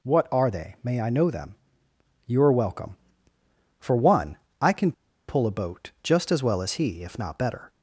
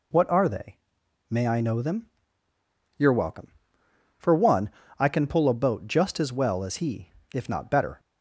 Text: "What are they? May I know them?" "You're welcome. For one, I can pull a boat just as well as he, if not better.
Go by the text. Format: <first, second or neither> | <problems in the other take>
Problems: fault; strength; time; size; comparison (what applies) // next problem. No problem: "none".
second | pauses between "can" and "pull"; at 4.9 s; 0.36 s long